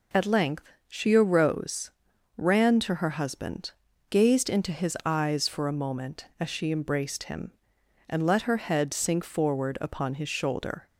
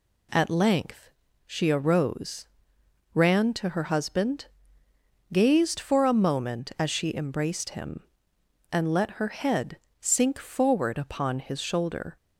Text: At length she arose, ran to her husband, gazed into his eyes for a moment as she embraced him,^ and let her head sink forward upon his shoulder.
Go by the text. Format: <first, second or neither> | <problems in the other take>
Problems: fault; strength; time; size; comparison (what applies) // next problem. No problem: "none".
first | pauses between "length" and "she"; slight; at 1.0 s; 0.34 s long; slight in the first // skips "into his eyes"; at 5.8 s // pauses between "head" and "sink"; slight; at 9.7 s; 0.24 s long